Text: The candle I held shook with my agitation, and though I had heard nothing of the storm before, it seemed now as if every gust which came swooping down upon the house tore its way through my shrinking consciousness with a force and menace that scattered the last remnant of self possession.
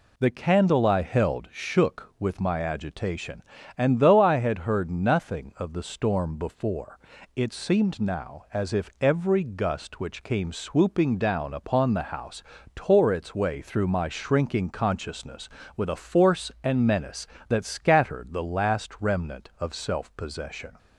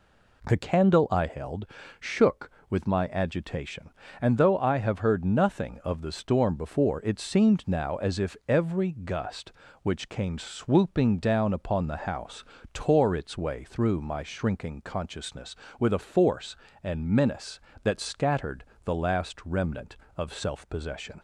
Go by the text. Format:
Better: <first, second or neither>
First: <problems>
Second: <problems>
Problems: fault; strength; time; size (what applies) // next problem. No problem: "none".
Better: first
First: pauses between "house" and "tore"; slight; at 12.4 s; 0.32 s long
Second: pauses between "held" and "shook"; slight; at 1.6 s; 0.34 s long // says "have" for "had"; at 4.7 s // pauses between "house" and "tore"; slight; at 12.4 s; 0.28 s long // pauses between "scattered" and "the"; slight; at 18.6 s; 0.20 s long